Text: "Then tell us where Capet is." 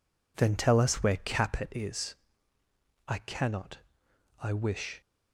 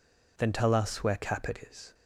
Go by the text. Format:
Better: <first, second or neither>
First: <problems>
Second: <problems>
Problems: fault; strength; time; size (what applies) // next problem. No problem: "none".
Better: second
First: goes on to say "I cannot I wish"; strong; from 3.0 s on; 1.9 s long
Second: none